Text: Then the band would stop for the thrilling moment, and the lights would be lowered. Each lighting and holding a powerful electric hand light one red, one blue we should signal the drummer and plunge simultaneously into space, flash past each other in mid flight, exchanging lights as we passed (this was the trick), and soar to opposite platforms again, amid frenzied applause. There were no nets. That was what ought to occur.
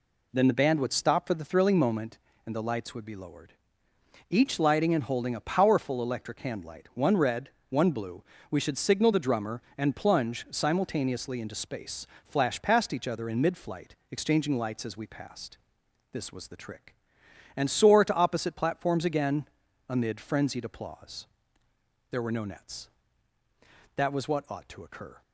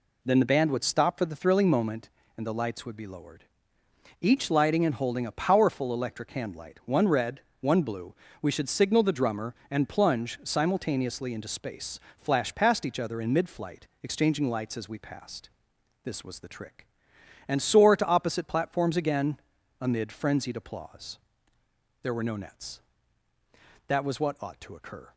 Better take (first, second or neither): neither